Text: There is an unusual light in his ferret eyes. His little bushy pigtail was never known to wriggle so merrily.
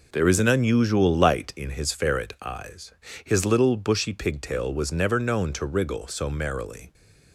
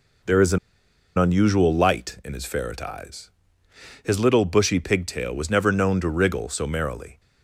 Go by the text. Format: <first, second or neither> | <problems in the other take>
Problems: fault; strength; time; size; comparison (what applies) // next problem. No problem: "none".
first | pauses between "an" and "unusual"; noticeable; at 0.5 s; 0.59 s long